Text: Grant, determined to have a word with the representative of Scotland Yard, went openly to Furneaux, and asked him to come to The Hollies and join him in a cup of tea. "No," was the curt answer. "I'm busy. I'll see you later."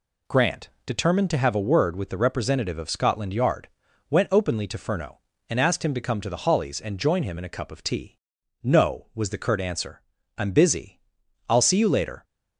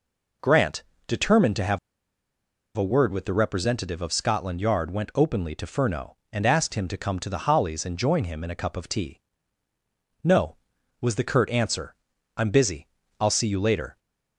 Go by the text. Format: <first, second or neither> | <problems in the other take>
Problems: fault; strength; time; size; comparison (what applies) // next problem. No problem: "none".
first | pauses between "have" and "a"; at 1.7 s; 0.99 s long